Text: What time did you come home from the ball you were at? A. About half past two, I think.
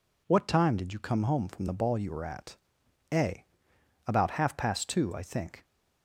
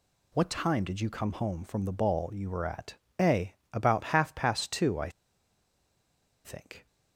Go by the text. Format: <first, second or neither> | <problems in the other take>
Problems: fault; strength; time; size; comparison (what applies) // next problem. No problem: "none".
first | pauses between "I" and "think"; strong; at 5.0 s; 1.3 s long